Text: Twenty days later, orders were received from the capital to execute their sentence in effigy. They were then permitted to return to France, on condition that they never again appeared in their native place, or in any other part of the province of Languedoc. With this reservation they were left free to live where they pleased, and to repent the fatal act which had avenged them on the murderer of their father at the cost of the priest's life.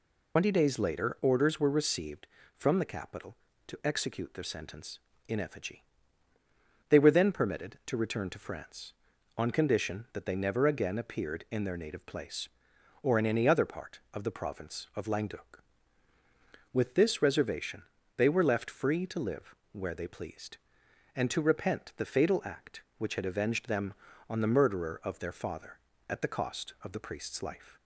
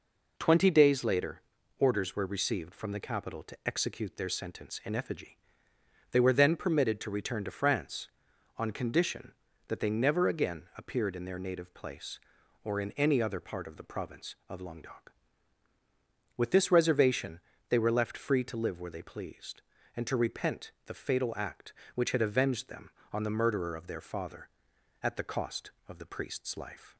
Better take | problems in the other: second | loses the start of "Twenty"; at 0.3 s; 110 ms // pauses between "reservation" and "they"; slight; at 17.8 s; 0.34 s long; slight in the second // pauses between "live" and "where"; slight; at 19.5 s; 0.18 s long

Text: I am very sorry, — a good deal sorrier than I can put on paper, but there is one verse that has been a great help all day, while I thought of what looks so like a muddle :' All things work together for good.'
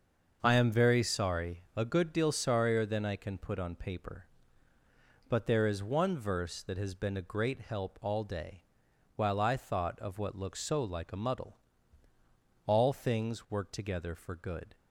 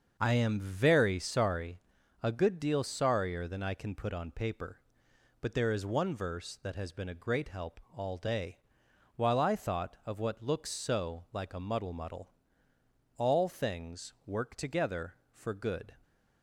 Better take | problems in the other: first | starts louder than the rest; until 1.2 s; 6.5 dB; also in the first // pauses between "help" and "all"; slight; at 7.7 s; 0.16 s long // says "muddle" twice; at 11.9 s

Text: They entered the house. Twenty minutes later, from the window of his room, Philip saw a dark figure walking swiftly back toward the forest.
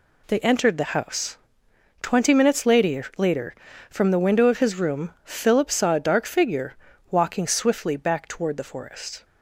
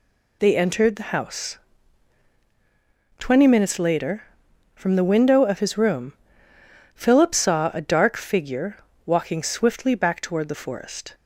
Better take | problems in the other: second | says "later" twice; at 3.1 s // pauses between "figure" and "walking"; at 6.7 s; 0.38 s long; slight in the second

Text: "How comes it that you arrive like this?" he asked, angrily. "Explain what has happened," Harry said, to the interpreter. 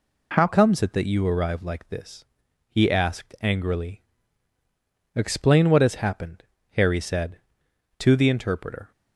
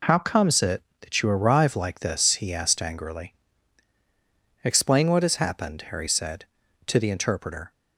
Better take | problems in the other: second | changes voice at "comes"; from 0.4 s on; 8.5 s long

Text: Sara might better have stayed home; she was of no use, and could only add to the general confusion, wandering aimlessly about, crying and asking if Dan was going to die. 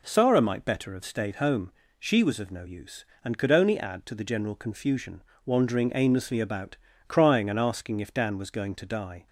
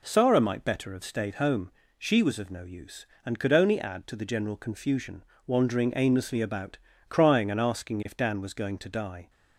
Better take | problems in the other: neither | none

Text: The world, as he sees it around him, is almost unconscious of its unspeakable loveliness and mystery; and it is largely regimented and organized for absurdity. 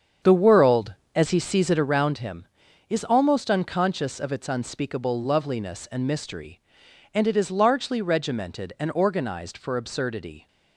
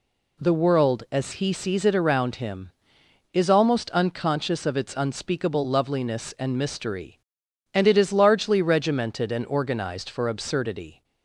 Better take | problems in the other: second | starts louder than the rest; strong; until 2.1 s; 7.5 dB

